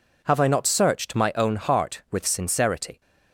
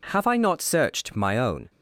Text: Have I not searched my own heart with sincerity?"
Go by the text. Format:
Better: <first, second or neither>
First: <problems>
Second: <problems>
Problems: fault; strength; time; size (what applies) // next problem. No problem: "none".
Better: first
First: none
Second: stops before "heart with sincerity"; at 1.6 s